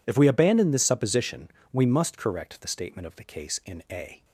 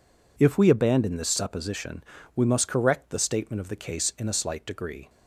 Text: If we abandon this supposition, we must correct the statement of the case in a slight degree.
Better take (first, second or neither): second